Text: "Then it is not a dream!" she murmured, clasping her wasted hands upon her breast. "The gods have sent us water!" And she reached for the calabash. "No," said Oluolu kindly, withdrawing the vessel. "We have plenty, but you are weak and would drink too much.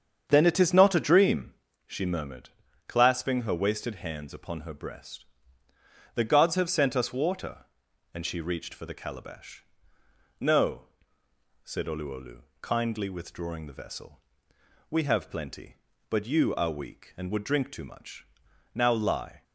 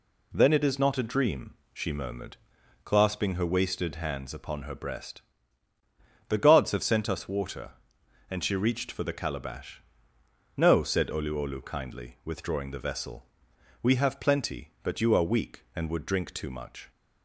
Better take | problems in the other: second | starts louder than the rest; strong; until 1.2 s; 7.5 dB // pauses between "Oluolu" and "kindly"; slight; at 12.4 s; 0.18 s long // goes on to say "Now lie"; noticeable; from 18.7 s on; 0.68 s long

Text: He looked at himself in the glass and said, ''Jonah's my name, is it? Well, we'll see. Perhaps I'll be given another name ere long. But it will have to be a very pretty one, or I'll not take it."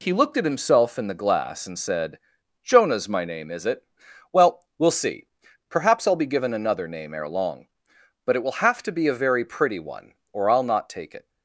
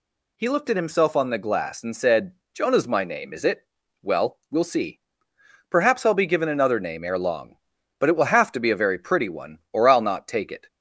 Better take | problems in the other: first | says "on" for "in"; at 1.1 s

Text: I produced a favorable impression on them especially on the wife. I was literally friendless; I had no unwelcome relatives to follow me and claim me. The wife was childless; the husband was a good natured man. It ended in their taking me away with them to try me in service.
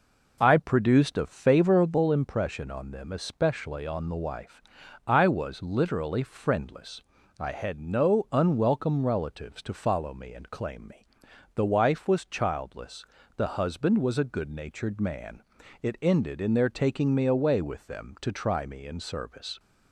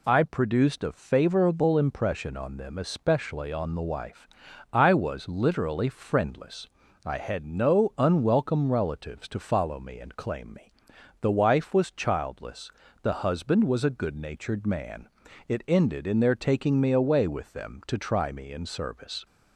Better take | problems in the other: second | starts louder than the rest; noticeable; until 2.0 s; 4.5 dB

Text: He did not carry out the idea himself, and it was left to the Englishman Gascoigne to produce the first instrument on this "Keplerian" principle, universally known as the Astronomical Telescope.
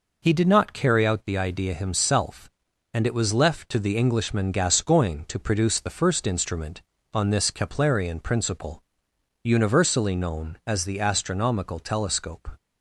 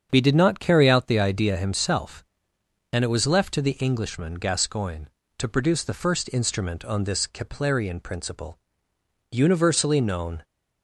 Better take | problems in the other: first | starts louder than the rest; strong; until 1.1 s; 7 dB // stops before "as the Astronomical Telescope"; at 10.4 s

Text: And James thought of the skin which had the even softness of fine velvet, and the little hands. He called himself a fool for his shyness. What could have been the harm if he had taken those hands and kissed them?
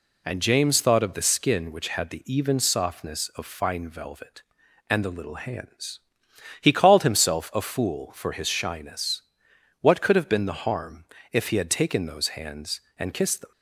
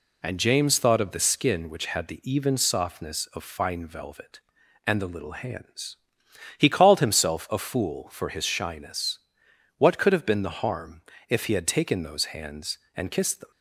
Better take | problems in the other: neither | pauses between "harm" and "if"; slight; the same in both

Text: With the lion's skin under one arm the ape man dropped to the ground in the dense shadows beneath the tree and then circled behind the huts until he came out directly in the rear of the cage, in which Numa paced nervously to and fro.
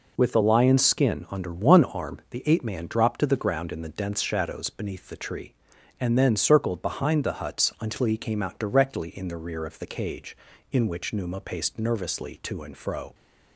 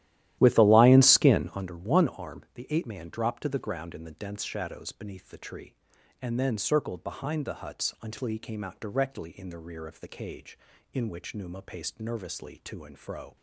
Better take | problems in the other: first | starts louder than the rest; strong; until 1.7 s; 13.5 dB

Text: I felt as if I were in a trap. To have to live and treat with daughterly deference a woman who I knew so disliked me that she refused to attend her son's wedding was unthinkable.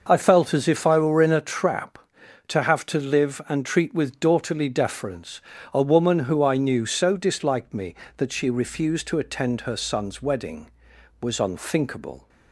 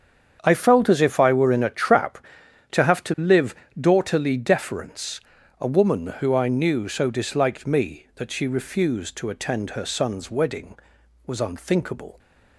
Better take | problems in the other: first | starts louder than the rest; strong; until 1.4 s; 7.5 dB // skips "and treat with"; at 3.6 s // pauses between "deference" and "a"; at 5.2 s; 0.40 s long; slight in the first

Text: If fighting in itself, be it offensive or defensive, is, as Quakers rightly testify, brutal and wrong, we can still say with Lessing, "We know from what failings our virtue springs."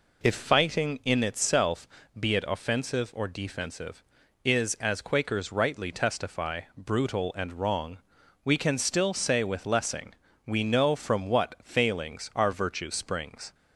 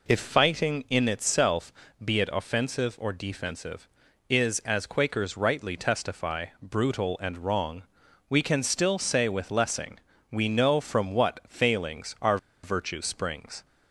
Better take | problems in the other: first | pauses between "our" and "virtue"; slight; at 12.3 s; 0.26 s long

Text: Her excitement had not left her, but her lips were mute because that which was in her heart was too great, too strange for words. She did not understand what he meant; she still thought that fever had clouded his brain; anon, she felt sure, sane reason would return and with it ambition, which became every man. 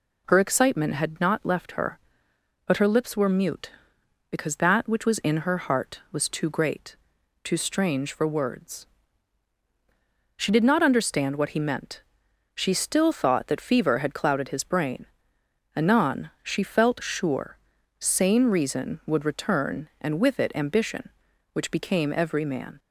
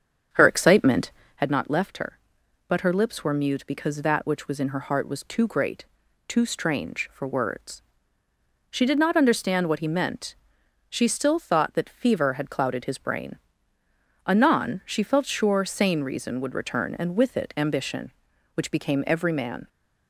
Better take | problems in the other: first | starts louder than the rest; strong; until 1.4 s; 7.5 dB

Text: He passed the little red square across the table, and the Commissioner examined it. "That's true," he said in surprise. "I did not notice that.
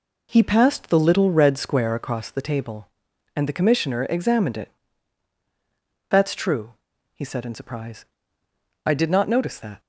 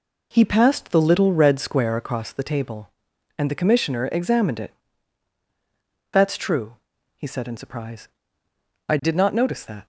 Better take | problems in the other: neither | none

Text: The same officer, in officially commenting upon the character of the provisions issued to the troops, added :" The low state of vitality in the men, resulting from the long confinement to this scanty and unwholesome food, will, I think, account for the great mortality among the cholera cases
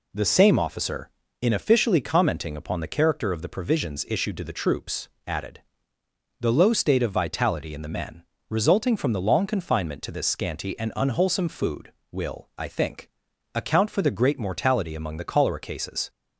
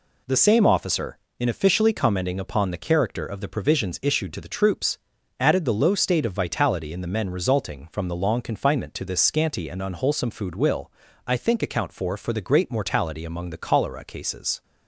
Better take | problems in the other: first | says "for" twice; at 12.1 s

